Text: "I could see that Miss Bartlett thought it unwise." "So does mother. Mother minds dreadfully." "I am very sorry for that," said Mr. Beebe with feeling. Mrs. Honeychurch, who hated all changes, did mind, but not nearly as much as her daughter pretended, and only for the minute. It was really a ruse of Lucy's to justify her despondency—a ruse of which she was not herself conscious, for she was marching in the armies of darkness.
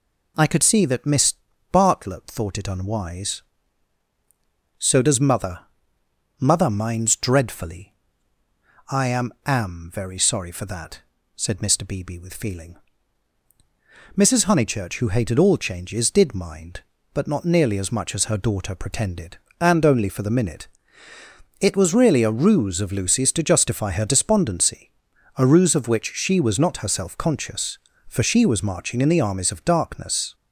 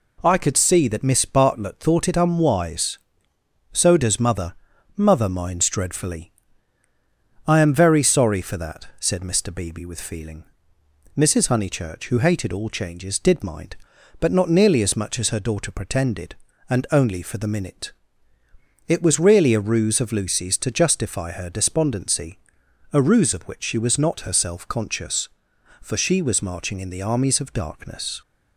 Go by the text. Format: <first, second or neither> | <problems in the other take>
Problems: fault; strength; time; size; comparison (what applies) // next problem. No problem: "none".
second | pauses between "Miss" and "Bartlett"; at 1.3 s; 0.38 s long // says "am" twice; at 9.4 s